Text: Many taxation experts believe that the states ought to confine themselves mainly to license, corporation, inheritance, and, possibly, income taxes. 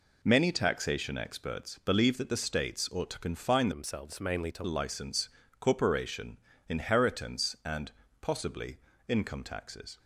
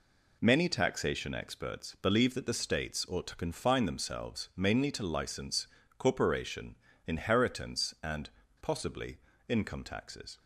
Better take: second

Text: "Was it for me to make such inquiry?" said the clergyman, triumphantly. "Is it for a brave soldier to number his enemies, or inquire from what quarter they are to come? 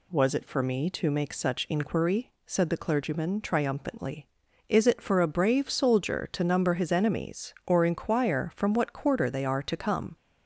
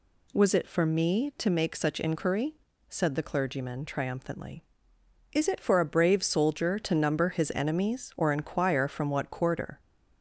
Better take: first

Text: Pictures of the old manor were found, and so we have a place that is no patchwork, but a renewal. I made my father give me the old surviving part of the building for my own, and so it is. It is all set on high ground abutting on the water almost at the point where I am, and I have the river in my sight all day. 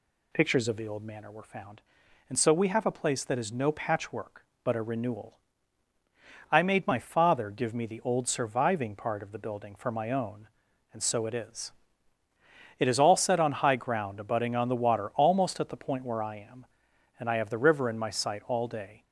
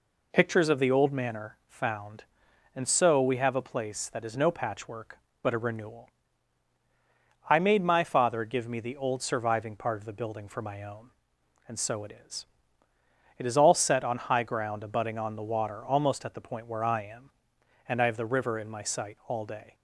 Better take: first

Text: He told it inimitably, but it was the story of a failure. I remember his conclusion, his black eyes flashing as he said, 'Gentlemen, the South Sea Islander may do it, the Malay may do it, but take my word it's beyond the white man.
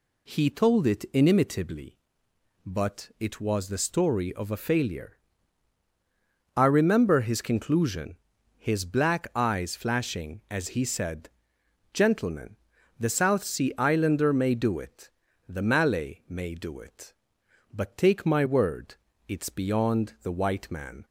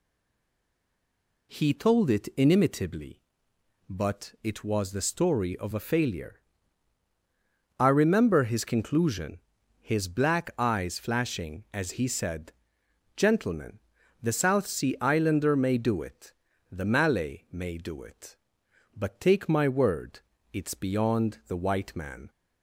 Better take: first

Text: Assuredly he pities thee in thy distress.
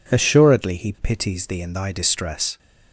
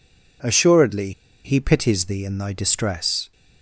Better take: first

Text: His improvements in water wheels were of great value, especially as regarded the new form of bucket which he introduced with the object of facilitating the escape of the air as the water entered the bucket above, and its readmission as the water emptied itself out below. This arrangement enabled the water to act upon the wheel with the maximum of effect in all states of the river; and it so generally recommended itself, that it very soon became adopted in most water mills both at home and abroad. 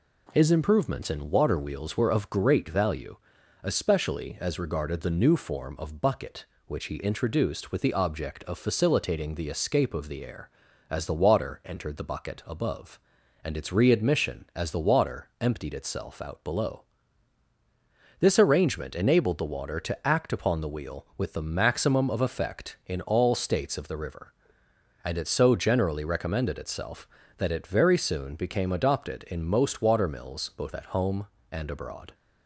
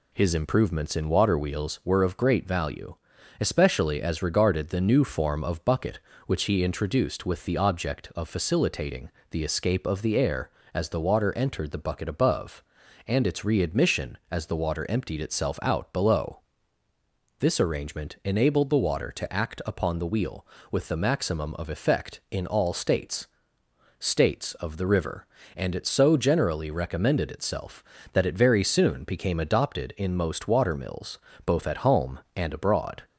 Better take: first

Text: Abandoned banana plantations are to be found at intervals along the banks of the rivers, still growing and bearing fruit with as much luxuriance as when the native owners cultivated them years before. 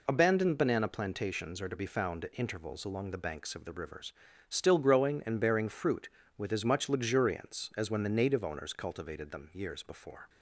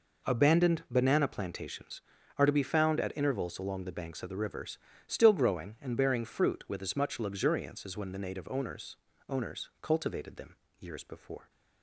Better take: first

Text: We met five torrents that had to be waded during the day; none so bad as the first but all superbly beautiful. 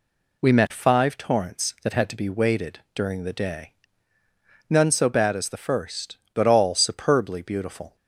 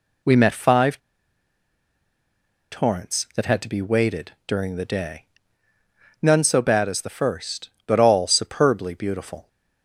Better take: first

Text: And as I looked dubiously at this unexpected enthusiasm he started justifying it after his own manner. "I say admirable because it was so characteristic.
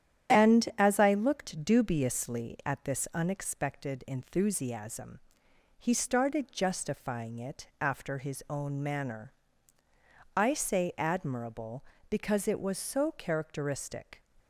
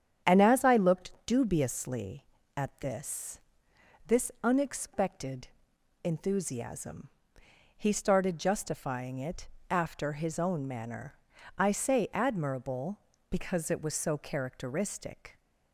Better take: first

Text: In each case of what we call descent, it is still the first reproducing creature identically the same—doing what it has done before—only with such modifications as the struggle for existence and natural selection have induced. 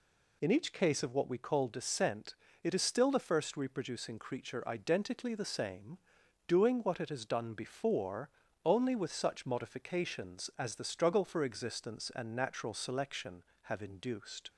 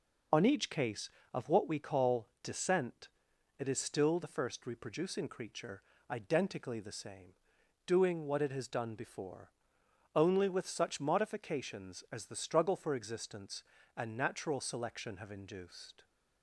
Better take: first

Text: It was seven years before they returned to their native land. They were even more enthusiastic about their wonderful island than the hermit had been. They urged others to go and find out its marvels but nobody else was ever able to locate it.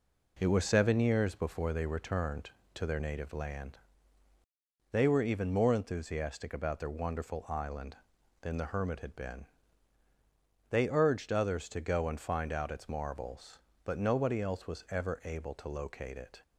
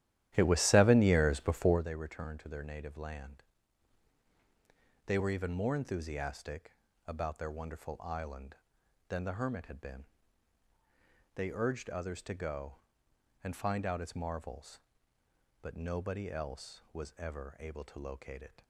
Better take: first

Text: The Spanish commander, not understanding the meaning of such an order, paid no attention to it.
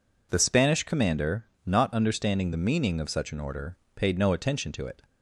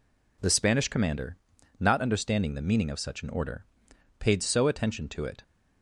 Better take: first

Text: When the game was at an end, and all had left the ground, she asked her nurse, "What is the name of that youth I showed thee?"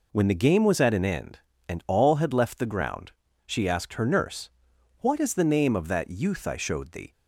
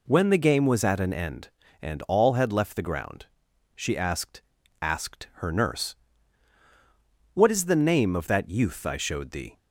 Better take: first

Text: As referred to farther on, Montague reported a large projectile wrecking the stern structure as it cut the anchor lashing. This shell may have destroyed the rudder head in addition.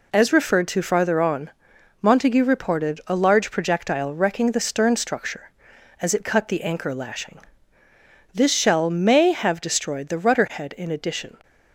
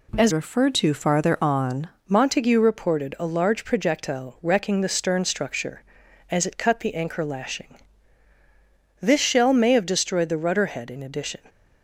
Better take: first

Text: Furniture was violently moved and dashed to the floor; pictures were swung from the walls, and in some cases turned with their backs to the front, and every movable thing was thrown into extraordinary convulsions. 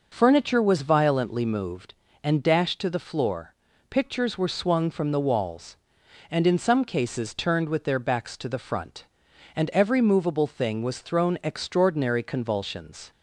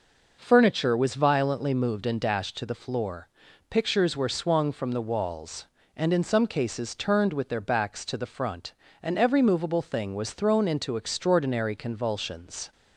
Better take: second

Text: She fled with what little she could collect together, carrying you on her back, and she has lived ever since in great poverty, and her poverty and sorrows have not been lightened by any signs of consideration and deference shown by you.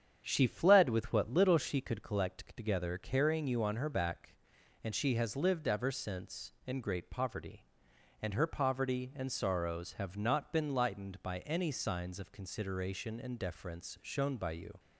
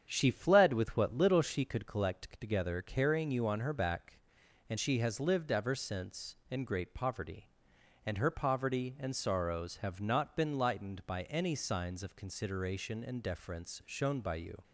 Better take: neither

